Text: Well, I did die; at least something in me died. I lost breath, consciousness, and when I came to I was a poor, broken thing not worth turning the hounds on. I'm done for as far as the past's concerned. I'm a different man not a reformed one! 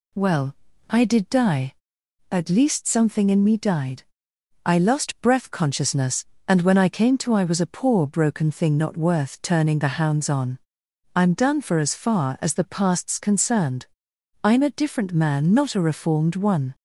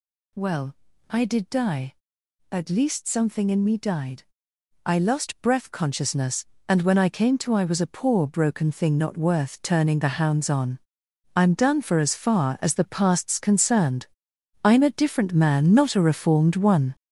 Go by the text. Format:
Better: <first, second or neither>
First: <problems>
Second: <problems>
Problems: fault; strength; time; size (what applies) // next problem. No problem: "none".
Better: first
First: none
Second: gets louder; strong; throughout; 8 dB